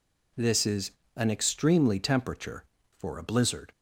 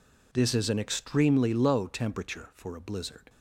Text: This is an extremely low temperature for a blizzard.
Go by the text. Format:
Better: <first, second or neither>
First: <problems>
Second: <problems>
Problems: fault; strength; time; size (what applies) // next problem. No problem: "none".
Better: second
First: pauses between "is" and "an"; slight; at 0.8 s; 0.26 s long // skips "low"; at 1.9 s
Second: none